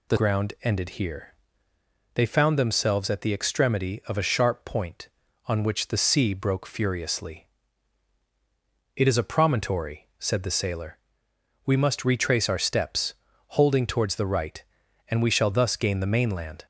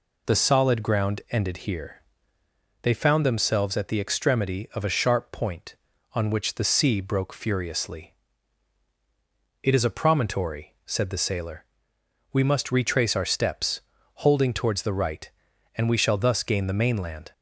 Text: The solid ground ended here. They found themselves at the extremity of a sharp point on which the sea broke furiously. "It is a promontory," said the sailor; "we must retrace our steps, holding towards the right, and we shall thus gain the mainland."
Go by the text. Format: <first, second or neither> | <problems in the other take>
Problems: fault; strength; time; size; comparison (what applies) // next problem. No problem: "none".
second | skips "solid"; at 0.1 s